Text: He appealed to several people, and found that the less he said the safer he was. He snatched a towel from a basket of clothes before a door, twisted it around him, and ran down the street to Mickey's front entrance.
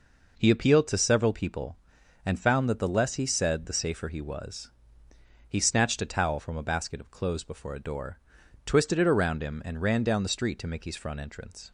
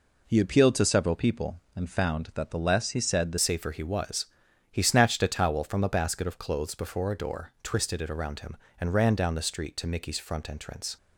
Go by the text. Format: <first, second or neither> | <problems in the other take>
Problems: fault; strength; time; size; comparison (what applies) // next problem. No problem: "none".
first | changes voice at "safer"; from 3.3 s on; 7.6 s long